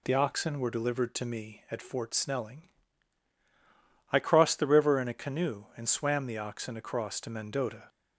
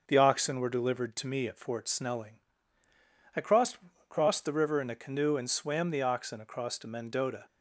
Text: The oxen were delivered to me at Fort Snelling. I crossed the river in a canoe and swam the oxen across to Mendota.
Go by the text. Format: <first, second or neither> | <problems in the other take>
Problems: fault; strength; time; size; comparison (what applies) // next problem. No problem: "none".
first | starts louder than the rest; until 1.0 s; 6.5 dB // says "crossed" twice; at 4.0 s